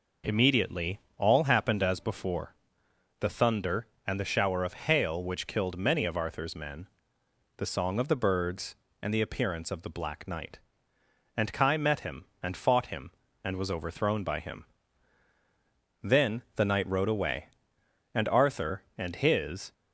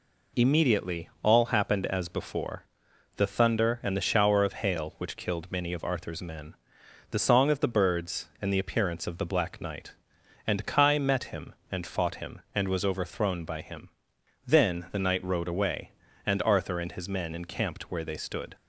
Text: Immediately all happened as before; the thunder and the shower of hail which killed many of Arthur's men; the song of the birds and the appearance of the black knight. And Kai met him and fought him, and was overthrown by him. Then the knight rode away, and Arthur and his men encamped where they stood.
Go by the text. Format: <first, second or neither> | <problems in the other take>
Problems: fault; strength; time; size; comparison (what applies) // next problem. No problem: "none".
second | pauses between "Immediately" and "all"; slight; at 0.9 s; 0.20 s long // pauses between "Then" and "the"; slight; at 16.4 s; 0.16 s long // stops before "men encamped where they stood"; at 19.7 s